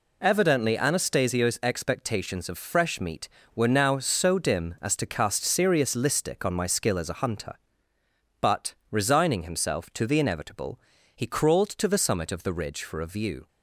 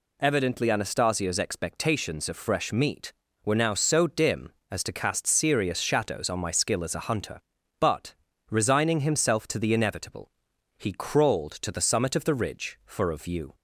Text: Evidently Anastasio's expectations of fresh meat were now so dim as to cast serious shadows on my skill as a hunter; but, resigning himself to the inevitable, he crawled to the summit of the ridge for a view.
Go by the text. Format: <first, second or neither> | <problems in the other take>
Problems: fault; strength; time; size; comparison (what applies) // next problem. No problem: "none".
second | says "listic" for "shadows"; at 5.9 s